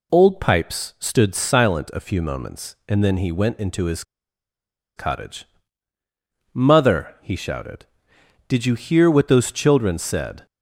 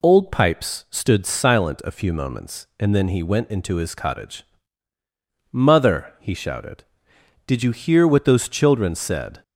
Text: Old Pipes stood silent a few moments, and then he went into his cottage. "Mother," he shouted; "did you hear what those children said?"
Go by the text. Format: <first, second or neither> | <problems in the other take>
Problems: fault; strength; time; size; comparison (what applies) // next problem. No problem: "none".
second | pauses between "his" and "cottage"; noticeable; at 4.0 s; 0.94 s long